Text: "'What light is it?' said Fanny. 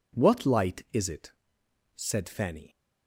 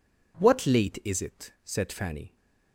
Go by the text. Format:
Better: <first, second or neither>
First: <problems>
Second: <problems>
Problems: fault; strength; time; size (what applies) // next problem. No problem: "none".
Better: first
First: none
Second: says "late" for "light"; at 0.6 s